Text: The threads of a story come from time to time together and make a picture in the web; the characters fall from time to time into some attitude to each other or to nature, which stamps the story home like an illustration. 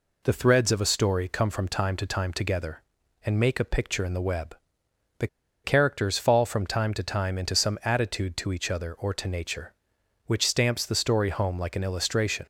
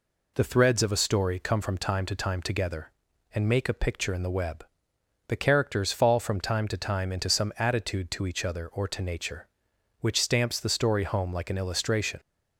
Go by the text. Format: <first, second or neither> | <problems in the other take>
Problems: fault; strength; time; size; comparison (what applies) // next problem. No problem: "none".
second | pauses between "the" and "characters"; at 5.2 s; 0.37 s long